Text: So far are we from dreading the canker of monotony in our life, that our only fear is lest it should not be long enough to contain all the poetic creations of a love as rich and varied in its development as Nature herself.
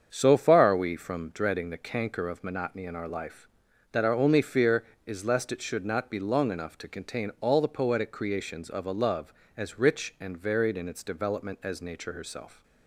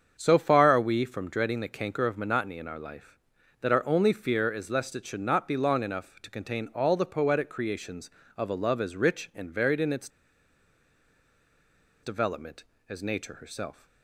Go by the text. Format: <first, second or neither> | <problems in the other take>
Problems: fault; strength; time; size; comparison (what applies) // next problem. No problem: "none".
first | starts louder than the rest; strong; until 1.2 s; 7 dB; strong in the first // pauses between "its" and "development"; strong; at 10.0 s; 1.9 s long